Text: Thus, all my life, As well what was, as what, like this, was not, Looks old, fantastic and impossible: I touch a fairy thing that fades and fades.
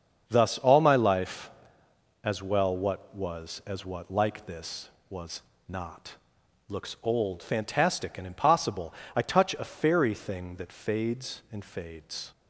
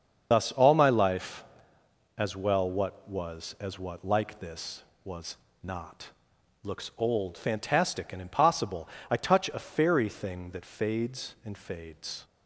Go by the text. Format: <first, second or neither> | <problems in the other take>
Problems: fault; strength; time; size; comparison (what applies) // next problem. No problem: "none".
first | loses the start of "Thus"; at 0.3 s; 85 ms // starts louder than the rest; until 1.3 s; 6.5 dB; also in the first // pauses between "was" and "not"; slight; at 5.3 s; 0.26 s long; slight in the first